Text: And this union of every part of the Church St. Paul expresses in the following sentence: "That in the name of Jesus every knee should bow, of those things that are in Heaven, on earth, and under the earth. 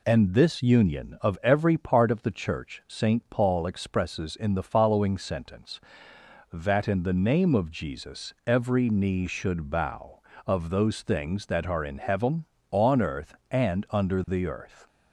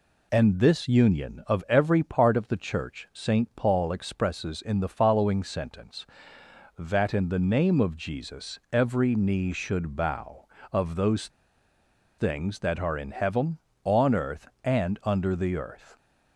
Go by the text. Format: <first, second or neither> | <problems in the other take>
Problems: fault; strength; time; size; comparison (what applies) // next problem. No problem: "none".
first | pauses between "those" and "things"; noticeable; at 11.2 s; 0.89 s long